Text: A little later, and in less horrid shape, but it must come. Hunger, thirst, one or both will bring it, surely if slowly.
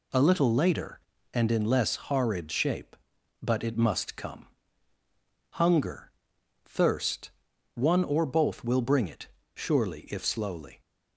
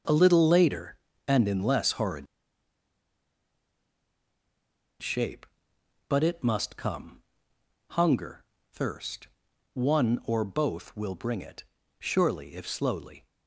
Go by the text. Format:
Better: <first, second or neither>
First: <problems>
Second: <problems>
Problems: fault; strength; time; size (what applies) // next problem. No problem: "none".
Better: first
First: none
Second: starts louder than the rest; until 1.4 s; 6.5 dB // pauses between "horrid" and "shape"; strong; at 2.2 s; 2.7 s long